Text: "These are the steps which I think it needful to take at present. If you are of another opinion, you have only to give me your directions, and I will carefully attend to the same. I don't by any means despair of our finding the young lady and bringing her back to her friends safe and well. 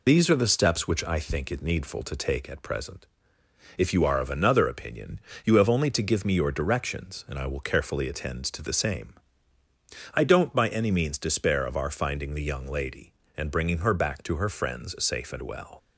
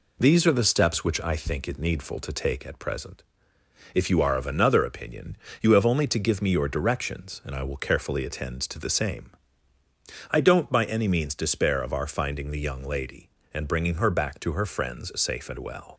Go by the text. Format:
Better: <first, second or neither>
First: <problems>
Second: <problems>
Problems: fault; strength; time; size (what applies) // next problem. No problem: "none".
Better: second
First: loses the start of "These"; at 0.0 s; 45 ms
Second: none